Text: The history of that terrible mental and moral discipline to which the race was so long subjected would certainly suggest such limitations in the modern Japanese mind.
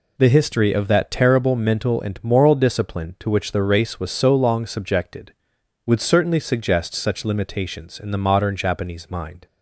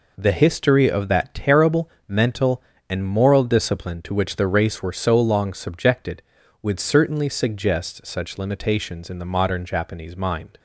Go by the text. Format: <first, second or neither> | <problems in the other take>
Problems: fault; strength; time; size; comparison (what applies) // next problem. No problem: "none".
first | pauses between "terrible" and "mental"; slight; at 1.9 s; 0.18 s long // says "were" for "was"; at 4.8 s